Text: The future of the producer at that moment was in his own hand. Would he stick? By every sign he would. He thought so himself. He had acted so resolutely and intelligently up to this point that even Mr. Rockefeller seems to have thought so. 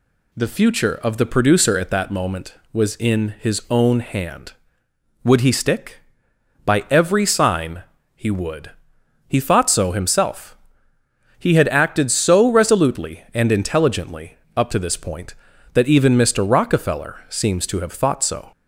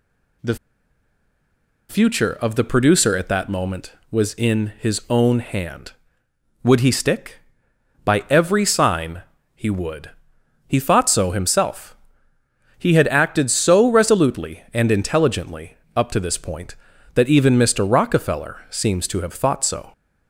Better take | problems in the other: first | pauses between "The" and "future"; strong; at 0.5 s; 1.3 s long // pauses between "sign" and "he"; slight; at 9.2 s; 0.32 s long; slight in the first // pauses between "intelligently" and "up"; slight; at 15.7 s; 0.18 s long; slight in the first

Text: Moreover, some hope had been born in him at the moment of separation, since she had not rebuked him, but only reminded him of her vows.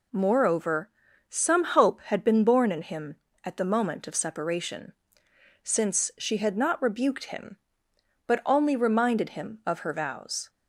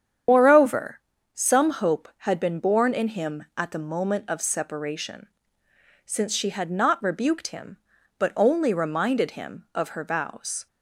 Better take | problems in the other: first | loses the start of "Moreover"; at 0.2 s; 120 ms // starts louder than the rest; strong; until 1.6 s; 8.5 dB

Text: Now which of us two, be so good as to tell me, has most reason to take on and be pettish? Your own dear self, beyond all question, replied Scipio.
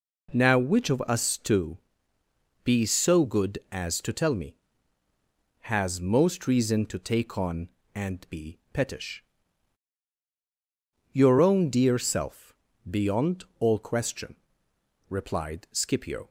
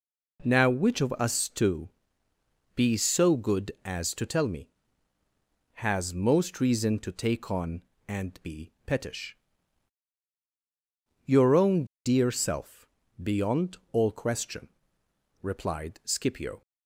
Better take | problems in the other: first | pauses between "be" and "pettish"; slight; at 8.7 s; 0.16 s long; slight in the first // pauses between "own" and "dear"; slight; at 11.8 s; 0.20 s long // pauses between "beyond" and "all"; slight; at 13.7 s; 0.16 s long; slight in the first

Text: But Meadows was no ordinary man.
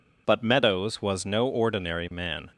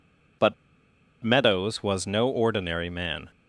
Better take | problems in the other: first | pauses between "But" and "Meadows"; noticeable; at 0.5 s; 0.70 s long

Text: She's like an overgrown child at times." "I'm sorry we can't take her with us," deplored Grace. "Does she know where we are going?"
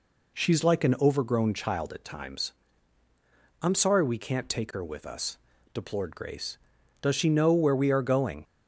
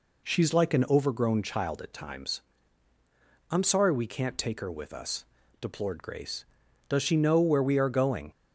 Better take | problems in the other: neither | none

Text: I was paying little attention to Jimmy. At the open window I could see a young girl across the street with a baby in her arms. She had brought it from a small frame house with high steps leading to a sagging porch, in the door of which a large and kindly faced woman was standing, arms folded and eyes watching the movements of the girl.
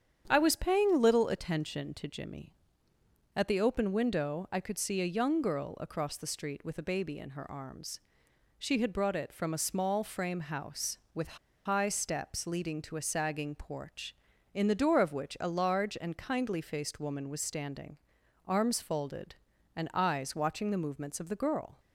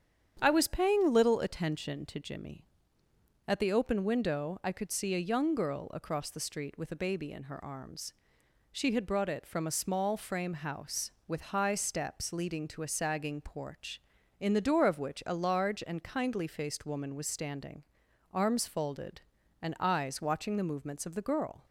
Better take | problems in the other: second | starts louder than the rest; strong; until 1.2 s; 8.5 dB; strong in the second // pauses between "with" and "high"; slight; at 11.3 s; 0.27 s long

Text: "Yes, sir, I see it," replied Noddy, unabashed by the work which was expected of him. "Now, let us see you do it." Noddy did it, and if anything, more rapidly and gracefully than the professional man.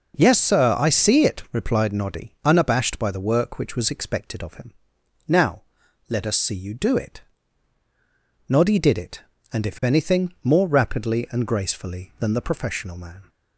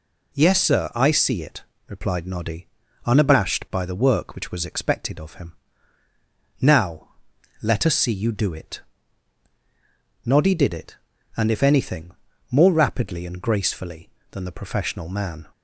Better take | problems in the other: neither | none

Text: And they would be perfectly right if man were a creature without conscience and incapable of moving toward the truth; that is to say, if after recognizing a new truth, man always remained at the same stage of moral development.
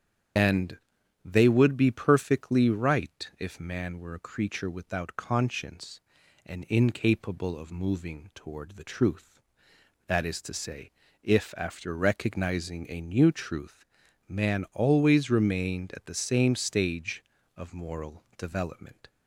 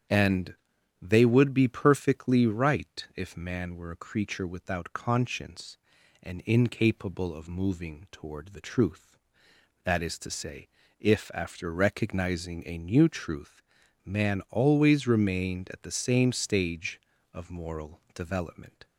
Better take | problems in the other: second | loses the start of "And"; at 0.3 s; 25 ms // starts louder than the rest; strong; until 1.8 s; 8.5 dB; strong in the second // pauses between "And" and "they"; noticeable; at 0.7 s; 0.48 s long; noticeable in the second

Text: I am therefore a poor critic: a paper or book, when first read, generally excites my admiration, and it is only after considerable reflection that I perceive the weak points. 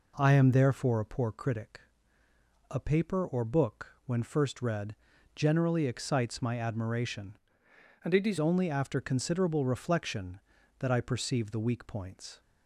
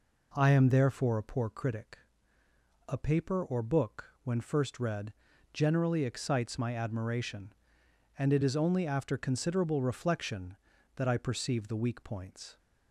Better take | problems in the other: second | changes voice from "and" to "is"; from 8.0 to 8.3 s; 0.3 s long

